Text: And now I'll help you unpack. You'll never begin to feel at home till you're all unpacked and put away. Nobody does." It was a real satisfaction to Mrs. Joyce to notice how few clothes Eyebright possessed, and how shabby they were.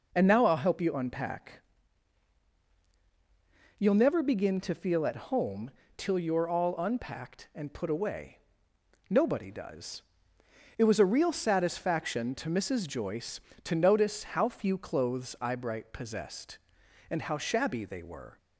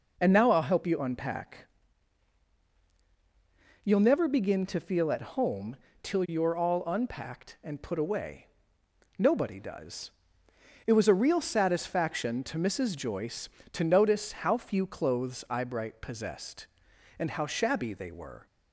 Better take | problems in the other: neither | pauses between "home" and "till"; slight; the same in both

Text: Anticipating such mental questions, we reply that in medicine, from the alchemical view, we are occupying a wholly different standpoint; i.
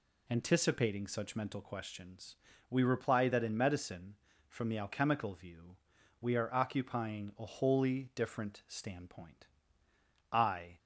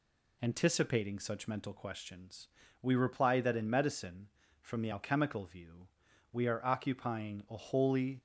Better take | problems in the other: first | stops before "different standpoint i"; at 8.1 s

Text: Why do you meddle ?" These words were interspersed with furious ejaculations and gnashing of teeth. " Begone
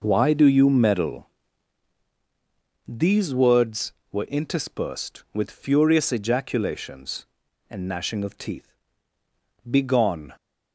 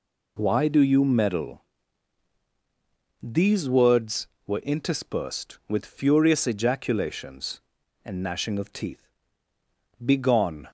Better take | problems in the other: second | starts louder than the rest; until 1.9 s; 6.5 dB

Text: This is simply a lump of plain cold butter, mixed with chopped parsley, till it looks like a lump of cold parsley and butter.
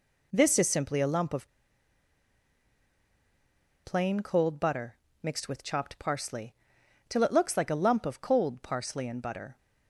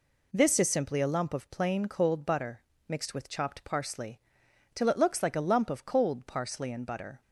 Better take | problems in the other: second | pauses between "of" and "plain"; strong; at 1.4 s; 2.3 s long

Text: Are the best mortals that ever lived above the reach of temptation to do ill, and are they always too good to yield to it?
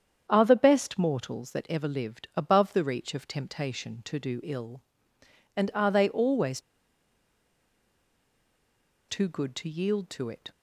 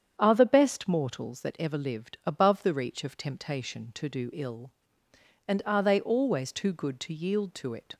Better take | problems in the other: second | starts louder than the rest; strong; until 1.3 s; 8 dB; strong in the second // pauses between "always" and "too"; strong; at 6.5 s; 2.4 s long

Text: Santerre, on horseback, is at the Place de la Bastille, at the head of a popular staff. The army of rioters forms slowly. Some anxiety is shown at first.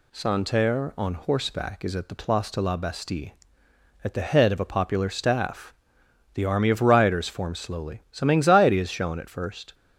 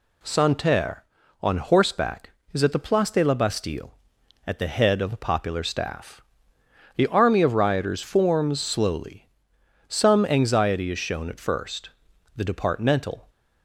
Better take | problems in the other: first | goes on to say "The departmental"; noticeable; from 12.3 s on; 0.94 s long

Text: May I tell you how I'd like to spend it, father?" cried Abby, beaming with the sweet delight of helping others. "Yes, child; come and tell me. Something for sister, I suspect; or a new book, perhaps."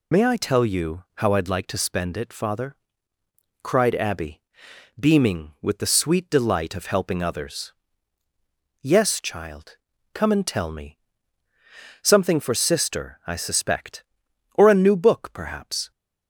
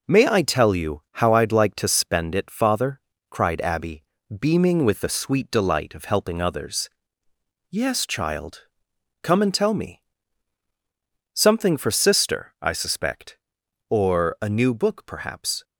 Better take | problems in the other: second | loses the start of "May"; at 0.1 s; 30 ms

